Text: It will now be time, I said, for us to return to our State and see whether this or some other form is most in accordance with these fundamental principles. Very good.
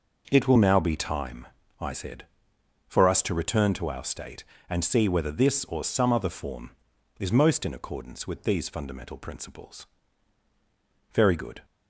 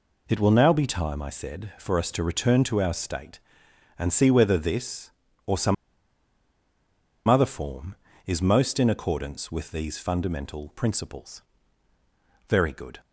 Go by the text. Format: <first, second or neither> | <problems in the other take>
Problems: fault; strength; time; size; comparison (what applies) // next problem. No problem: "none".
first | pauses between "some" and "other"; strong; at 5.7 s; 1.5 s long